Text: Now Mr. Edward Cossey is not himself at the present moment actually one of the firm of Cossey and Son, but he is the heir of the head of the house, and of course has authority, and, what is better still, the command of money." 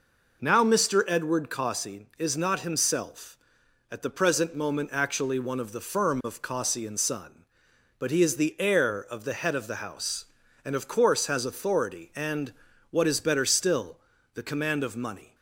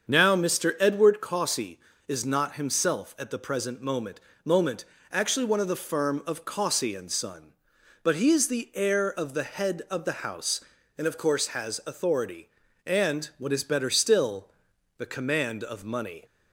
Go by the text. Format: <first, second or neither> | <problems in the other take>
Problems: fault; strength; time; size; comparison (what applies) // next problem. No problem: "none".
first | starts louder than the rest; until 1.1 s; 7 dB // says "moment" twice; at 4.4 s